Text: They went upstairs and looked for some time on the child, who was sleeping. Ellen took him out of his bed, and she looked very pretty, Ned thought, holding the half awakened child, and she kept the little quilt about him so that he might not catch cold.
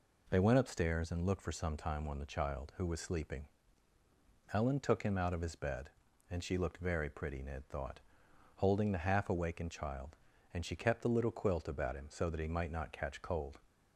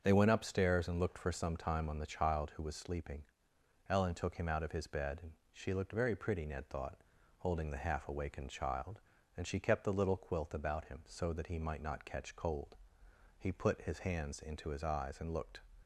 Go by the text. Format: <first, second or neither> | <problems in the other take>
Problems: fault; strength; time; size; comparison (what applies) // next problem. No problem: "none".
first | starts louder than the rest; until 1.0 s; 7 dB // pauses between "and" and "she"; slight; at 5.3 s; 0.18 s long // goes on to say "He put his hands into his eyes and looked"; strong; from 13.3 s on; 2.2 s long